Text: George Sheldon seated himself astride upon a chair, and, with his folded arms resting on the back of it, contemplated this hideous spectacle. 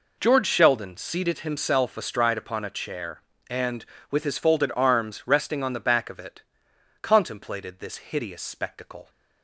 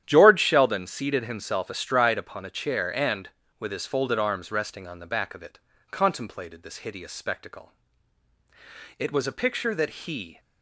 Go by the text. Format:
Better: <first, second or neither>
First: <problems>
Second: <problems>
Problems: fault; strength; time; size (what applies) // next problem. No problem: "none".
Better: first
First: none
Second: starts louder than the rest; strong; until 1.0 s; 10.5 dB // goes on to say "It was a picture that he"; from 8.9 s on; 1.4 s long